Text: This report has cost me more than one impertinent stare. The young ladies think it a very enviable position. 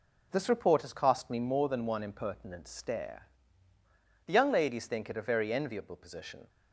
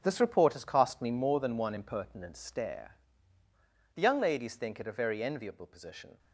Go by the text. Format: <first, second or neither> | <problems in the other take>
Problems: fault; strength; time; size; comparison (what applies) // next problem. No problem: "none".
first | gets quieter; strong; throughout; 10 dB